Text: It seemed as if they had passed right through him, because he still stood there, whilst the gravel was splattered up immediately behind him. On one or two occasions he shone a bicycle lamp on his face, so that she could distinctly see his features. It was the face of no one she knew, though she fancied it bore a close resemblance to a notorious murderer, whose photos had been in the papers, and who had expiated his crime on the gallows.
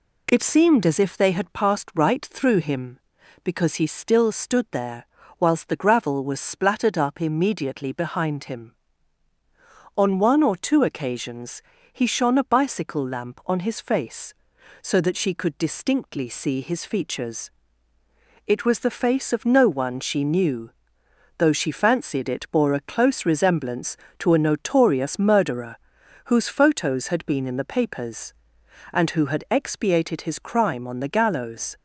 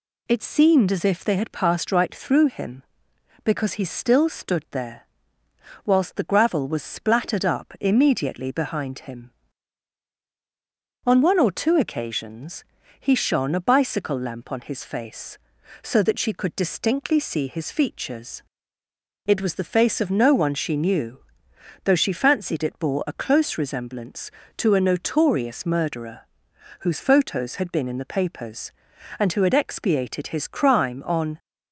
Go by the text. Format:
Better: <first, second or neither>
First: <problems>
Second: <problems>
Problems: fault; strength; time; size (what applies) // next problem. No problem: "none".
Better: first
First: pauses between "occasions" and "he"; slight; at 11.6 s; 0.28 s long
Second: pauses between "occasions" and "he"; slight; at 12.6 s; 0.34 s long // stops before "the gallows"; at 31.3 s